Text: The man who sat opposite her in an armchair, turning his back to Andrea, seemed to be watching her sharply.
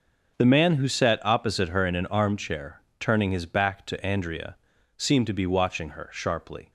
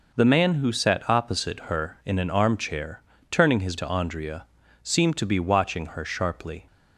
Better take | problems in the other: first | skips "back"; at 3.7 s

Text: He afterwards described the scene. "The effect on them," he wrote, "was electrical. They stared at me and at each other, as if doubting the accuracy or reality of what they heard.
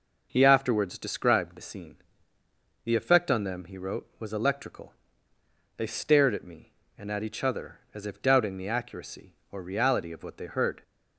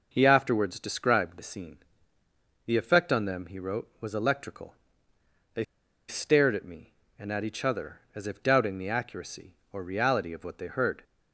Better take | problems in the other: first | pauses between "They" and "stared"; at 5.6 s; 0.44 s long

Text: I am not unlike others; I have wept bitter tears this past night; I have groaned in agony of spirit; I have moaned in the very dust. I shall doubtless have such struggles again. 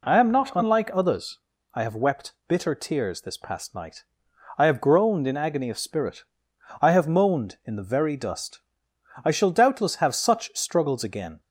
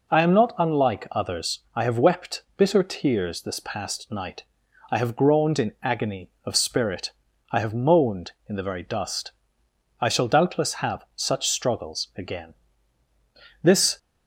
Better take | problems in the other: first | goes on to say "This"; slight; from 13.6 s on; 0.34 s long

